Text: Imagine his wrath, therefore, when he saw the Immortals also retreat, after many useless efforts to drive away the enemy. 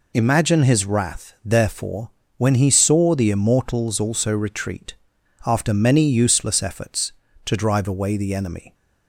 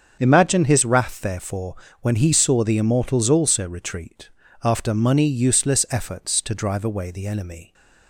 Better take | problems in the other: first | starts louder than the rest; until 1.2 s; 7 dB // says "money" for "many"; at 4.9 s

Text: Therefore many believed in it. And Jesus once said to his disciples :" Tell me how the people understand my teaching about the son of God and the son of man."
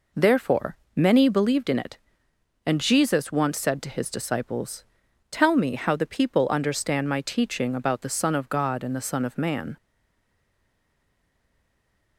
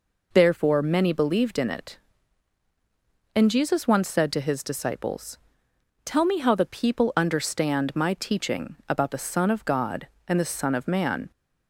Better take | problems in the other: second | pauses between "Therefore" and "many"; slight; at 0.7 s; 0.18 s long // stays silent after the last word; from 9.7 s on; 2.4 s long

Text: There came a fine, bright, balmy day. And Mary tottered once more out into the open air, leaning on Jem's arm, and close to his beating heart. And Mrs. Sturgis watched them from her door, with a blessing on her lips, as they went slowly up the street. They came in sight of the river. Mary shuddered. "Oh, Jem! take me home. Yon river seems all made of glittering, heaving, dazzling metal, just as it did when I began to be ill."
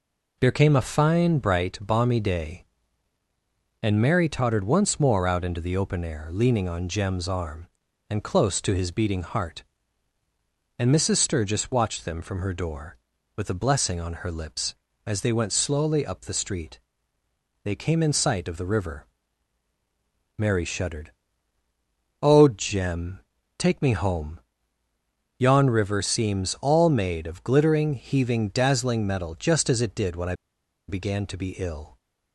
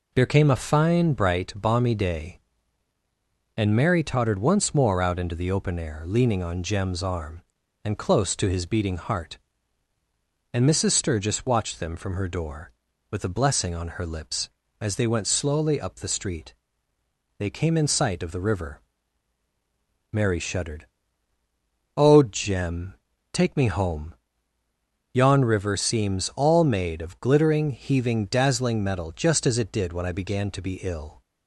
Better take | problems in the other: second | pauses between "I" and "began"; noticeable; at 30.3 s; 0.54 s long

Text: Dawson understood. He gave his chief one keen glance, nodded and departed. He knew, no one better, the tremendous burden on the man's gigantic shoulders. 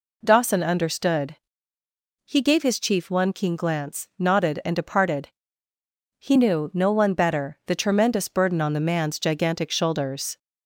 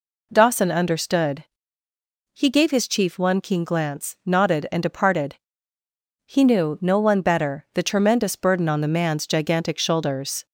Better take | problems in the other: neither | none

